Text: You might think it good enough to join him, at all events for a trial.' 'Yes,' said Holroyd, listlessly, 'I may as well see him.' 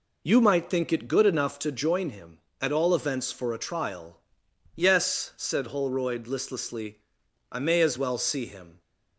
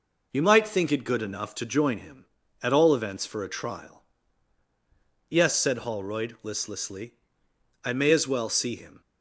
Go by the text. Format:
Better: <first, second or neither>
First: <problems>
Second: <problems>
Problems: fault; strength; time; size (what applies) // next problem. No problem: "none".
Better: neither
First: none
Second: none